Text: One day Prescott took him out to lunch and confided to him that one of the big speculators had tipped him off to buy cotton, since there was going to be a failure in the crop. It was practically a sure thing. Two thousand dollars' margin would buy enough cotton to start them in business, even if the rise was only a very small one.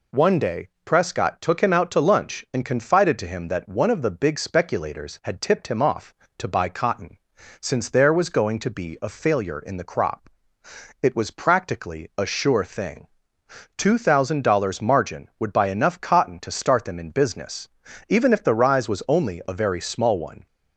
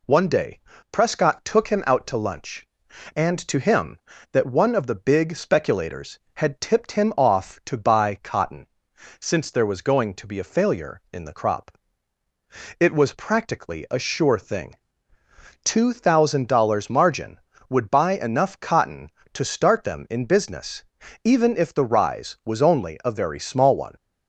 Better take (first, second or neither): first